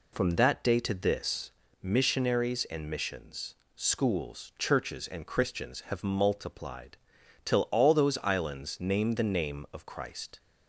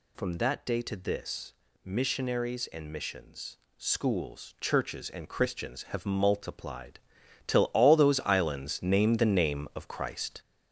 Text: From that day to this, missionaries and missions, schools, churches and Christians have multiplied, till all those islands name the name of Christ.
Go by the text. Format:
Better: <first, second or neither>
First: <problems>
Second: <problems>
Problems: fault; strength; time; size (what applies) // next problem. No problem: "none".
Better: first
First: none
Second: gets louder; noticeable; throughout; 5.5 dB